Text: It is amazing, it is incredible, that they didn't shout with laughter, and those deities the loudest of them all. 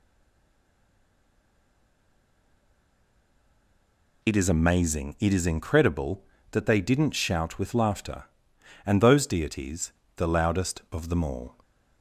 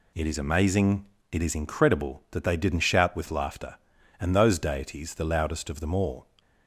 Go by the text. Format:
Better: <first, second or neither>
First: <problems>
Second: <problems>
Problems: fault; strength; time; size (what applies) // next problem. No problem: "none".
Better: second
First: stays silent before the first word; strong; until 4.2 s; 4.2 s long // pauses between "deities" and "the"; slight; at 9.9 s; 0.23 s long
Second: none